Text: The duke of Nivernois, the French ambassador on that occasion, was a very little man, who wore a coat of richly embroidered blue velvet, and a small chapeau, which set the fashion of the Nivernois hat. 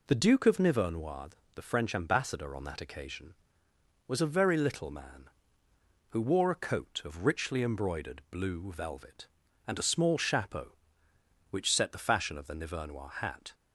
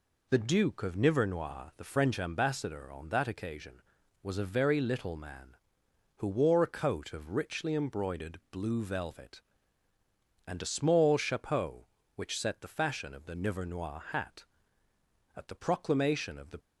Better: first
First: none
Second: goes on to say "At the proclamation of the"; noticeable; from 15.3 s on; 1.2 s long

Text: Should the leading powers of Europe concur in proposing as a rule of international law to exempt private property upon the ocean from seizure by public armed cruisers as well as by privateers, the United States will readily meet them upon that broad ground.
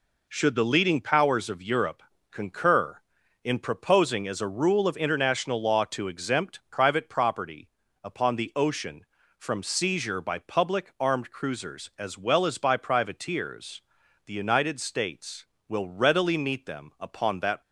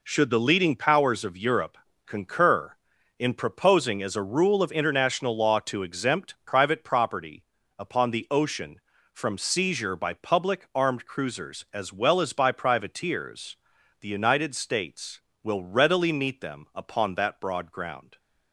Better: second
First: pauses between "Europe" and "concur"; slight; at 2.0 s; 0.28 s long // pauses between "property" and "upon"; slight; at 7.6 s; 0.36 s long // stops before "broad ground"; at 17.6 s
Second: pauses between "Europe" and "concur"; slight; at 1.7 s; 0.28 s long // pauses between "property" and "upon"; slight; at 7.4 s; 0.36 s long

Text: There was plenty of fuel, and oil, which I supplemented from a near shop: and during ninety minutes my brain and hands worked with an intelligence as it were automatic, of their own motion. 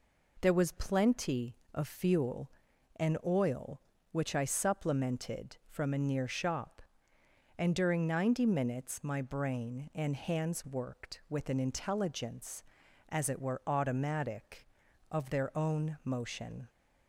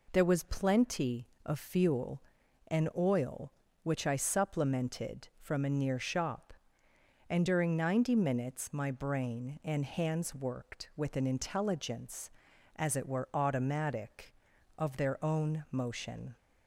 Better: neither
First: none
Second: none

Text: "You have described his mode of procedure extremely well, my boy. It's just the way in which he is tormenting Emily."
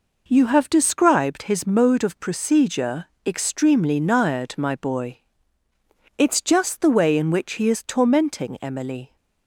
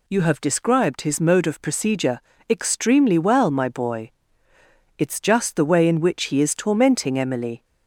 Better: second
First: pauses between "procedure" and "extremely"; slight; at 3.0 s; 0.18 s long // says "nired" for "well"; at 3.9 s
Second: pauses between "procedure" and "extremely"; slight; at 2.2 s; 0.28 s long

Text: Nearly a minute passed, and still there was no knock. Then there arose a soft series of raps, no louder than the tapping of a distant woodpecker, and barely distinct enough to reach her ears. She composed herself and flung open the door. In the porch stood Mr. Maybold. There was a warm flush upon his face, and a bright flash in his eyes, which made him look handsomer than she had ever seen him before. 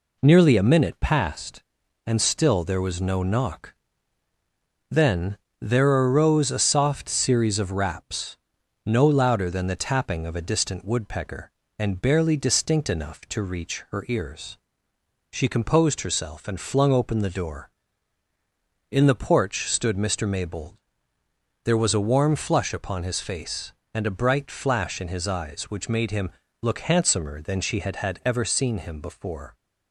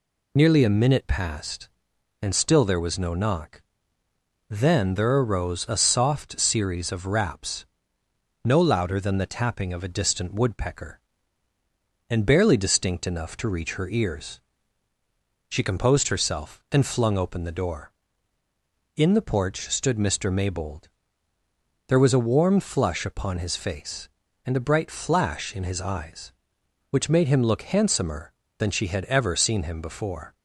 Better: second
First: pauses between "Then" and "there"; slight; at 5.3 s; 0.22 s long // pauses between "him" and "look"; slight; at 26.3 s; 0.28 s long // says "had" twice; at 27.9 s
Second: none

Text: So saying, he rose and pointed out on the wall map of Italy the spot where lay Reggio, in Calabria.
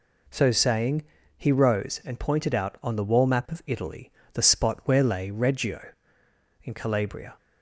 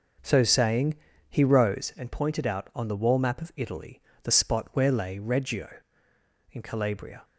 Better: first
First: pauses between "Italy" and "the"; slight; at 4.1 s; 0.22 s long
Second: starts louder than the rest; noticeable; until 2.0 s; 5.5 dB // pauses between "Italy" and "the"; slight; at 4.0 s; 0.22 s long

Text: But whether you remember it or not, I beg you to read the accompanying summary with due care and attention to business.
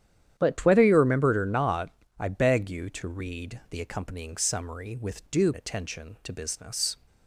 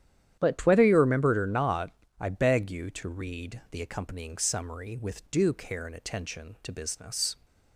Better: second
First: starts louder than the rest; strong; until 1.3 s; 10 dB // skips "care and"; at 5.5 s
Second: starts louder than the rest; strong; until 1.3 s; 10.5 dB

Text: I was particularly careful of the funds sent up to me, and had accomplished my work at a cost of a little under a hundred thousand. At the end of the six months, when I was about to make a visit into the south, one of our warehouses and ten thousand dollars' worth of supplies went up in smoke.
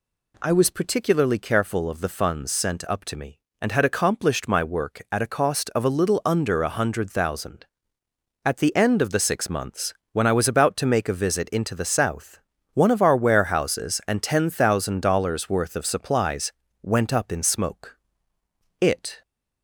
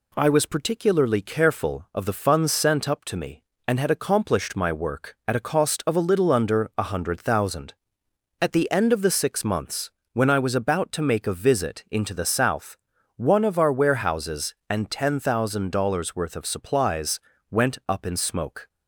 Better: second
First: pauses between "supplies" and "went"; slight; at 16.5 s; 0.30 s long // goes on to say "It"; slight; from 18.8 s on; 0.40 s long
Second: pauses between "supplies" and "went"; slight; at 17.1 s; 0.30 s long

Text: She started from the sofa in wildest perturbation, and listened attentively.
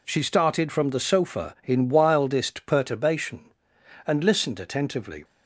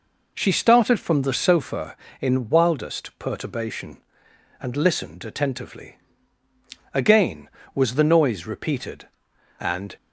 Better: first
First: none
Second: goes on to say "Again was the noise repeated and"; strong; from 6.9 s on; 3.0 s long

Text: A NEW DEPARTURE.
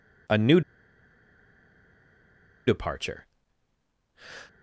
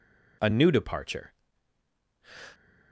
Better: second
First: pauses between "NEW" and "DEPARTURE"; strong; at 0.6 s; 2.0 s long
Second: none

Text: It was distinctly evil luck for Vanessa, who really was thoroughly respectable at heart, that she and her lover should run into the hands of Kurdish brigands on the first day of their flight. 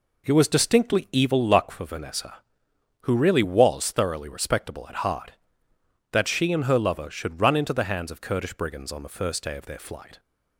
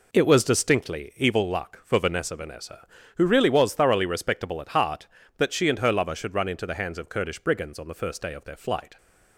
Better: first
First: none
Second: says "Vanessa" twice; at 2.3 s

